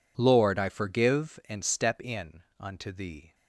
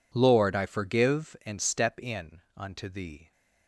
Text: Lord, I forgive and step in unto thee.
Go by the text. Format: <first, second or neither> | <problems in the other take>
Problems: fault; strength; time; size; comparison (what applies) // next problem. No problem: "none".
neither | pauses between "in" and "unto"; slight; the same in both